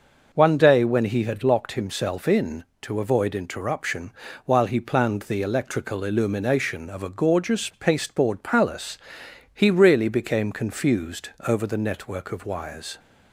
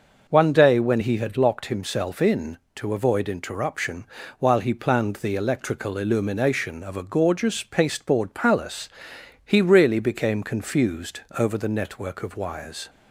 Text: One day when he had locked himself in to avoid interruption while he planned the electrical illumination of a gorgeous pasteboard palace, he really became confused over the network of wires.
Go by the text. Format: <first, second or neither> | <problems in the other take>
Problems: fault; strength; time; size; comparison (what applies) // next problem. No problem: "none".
neither | pauses between "interruption" and "while"; slight; the same in both // pauses between "confused" and "over"; slight; the same in both